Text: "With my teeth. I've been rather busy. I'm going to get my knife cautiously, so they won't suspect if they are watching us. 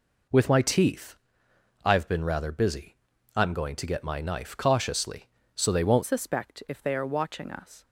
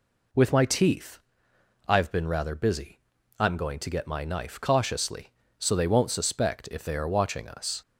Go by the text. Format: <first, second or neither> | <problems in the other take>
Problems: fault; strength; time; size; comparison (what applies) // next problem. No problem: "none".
second | changes voice at "suspect"; from 6.0 s on; 1.8 s long